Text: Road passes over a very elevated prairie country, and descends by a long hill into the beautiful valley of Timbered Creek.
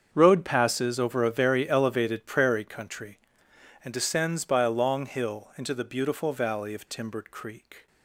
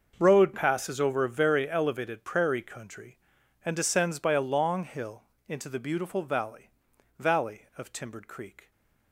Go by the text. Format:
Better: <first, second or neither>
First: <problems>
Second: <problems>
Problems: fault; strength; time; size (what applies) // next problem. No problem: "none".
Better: first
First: starts louder than the rest; strong; until 1.1 s; 7 dB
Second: starts louder than the rest; until 1.2 s; 6 dB // pauses between "hill" and "into"; slight; at 5.2 s; 0.24 s long // says "valley" twice; at 7.1 s